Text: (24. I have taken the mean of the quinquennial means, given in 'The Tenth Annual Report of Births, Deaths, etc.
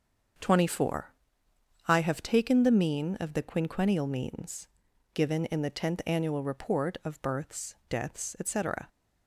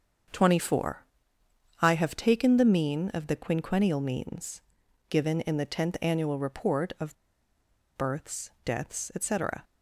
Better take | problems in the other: first | starts louder than the rest; until 2.0 s; 7 dB; also in the first // pauses between "of" and "Births"; noticeable; at 7.1 s; 0.81 s long

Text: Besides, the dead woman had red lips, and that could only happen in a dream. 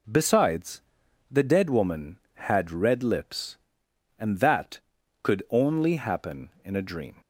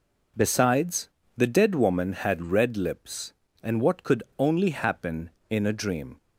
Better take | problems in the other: first | says "what" for "that"; at 3.8 s // pauses between "could" and "only"; slight; at 4.2 s; 0.16 s long

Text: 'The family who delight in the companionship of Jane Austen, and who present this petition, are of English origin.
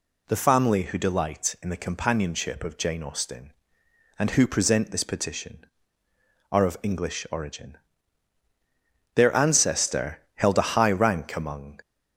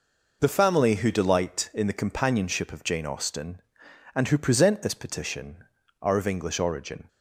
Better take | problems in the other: second | goes on to say "Their ancestor held a high rank among"; strong; from 9.1 s on; 2.6 s long

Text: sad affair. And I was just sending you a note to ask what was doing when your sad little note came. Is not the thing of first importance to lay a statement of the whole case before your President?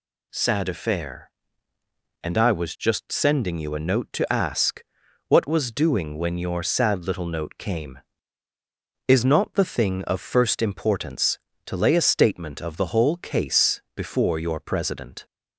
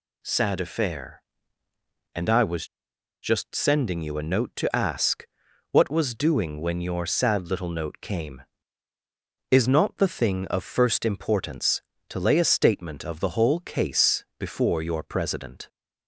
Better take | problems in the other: first | pauses between "was" and "just"; noticeable; at 2.6 s; 0.58 s long // pauses between "ask" and "what"; noticeable; at 5.2 s; 0.46 s long; noticeable in the first

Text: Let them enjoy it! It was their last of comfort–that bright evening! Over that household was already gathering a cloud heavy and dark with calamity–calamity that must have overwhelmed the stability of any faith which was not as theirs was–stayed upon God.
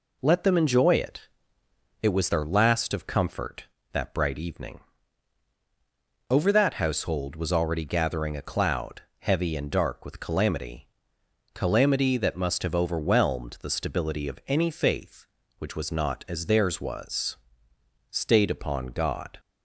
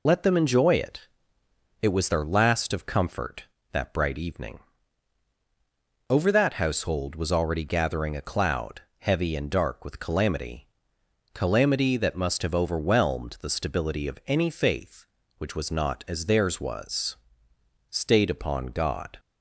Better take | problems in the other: first | loses the start of "Let"; at 0.0 s; 50 ms // pauses between "cloud" and "heavy"; slight; at 8.8 s; 0.18 s long; slight in the first

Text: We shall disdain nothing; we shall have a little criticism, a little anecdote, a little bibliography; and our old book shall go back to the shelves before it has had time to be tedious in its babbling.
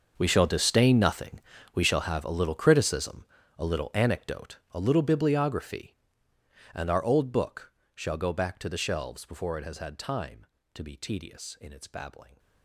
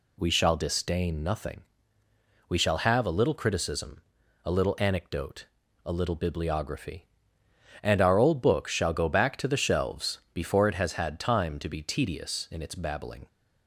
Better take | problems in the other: second | gets quieter; strong; throughout; 17.5 dB // pauses between "book" and "shall"; slight; at 7.7 s; 0.24 s long

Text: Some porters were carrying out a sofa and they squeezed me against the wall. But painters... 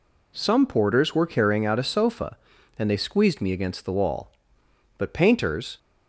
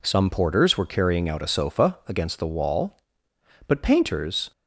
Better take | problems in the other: first | skips "and they squeezed me"; at 2.0 s

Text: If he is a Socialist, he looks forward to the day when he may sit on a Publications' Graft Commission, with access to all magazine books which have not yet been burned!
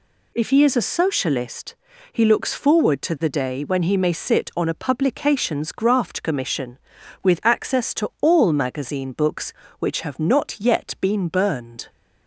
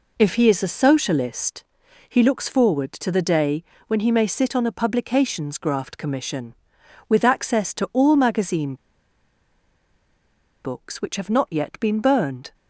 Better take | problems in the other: first | pauses between "day" and "when"; slight; at 3.6 s; 0.24 s long // pauses between "magazine" and "books"; strong; at 8.7 s; 1.8 s long

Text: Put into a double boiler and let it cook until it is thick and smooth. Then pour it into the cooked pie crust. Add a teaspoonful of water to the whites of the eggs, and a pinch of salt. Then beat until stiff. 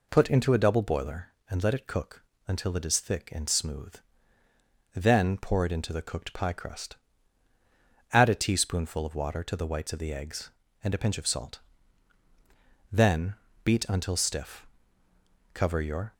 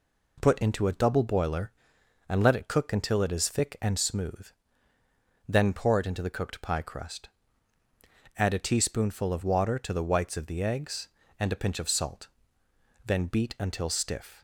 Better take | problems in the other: second | pauses between "cook" and "until"; slight; at 2.2 s; 0.24 s long // pauses between "Then" and "beat"; slight; at 13.3 s; 0.30 s long // goes on to say "Cover your"; from 15.5 s on; 0.60 s long

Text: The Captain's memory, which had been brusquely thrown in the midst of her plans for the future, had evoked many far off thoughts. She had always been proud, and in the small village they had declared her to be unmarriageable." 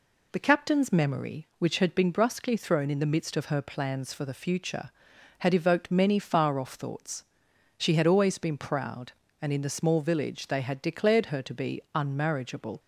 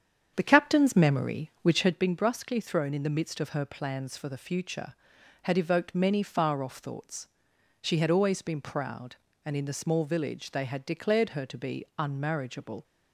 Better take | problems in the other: first | starts louder than the rest; strong; until 1.9 s; 8.5 dB

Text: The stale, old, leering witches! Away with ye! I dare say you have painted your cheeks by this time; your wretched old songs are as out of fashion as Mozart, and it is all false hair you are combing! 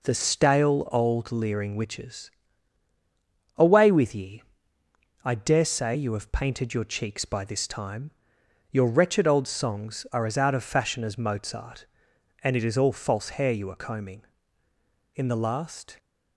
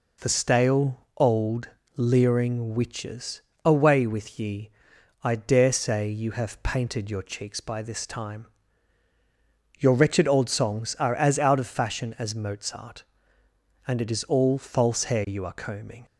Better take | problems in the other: second | goes on to say "In the last"; noticeable; from 15.1 s on; 0.82 s long

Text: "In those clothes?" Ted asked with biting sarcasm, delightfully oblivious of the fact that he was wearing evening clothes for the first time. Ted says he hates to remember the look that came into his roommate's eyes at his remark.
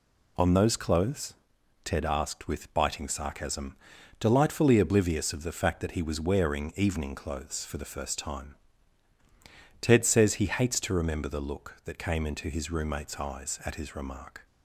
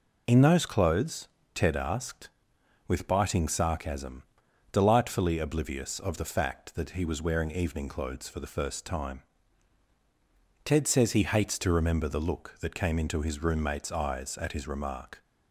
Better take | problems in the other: second | says "On" for "In"; at 0.3 s

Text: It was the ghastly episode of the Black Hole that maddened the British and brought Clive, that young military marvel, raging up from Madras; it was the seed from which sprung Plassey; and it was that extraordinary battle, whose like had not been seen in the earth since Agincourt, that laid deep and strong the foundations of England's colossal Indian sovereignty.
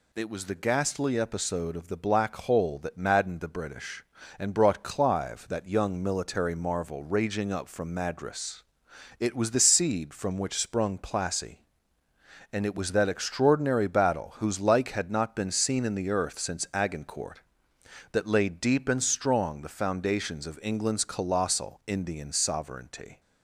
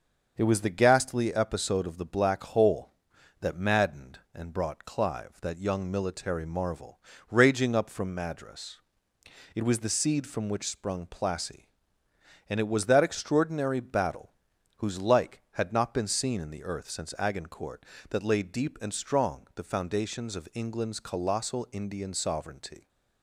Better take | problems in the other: first | starts louder than the rest; until 1.3 s; 6.5 dB // skips "the British"; at 4.2 s

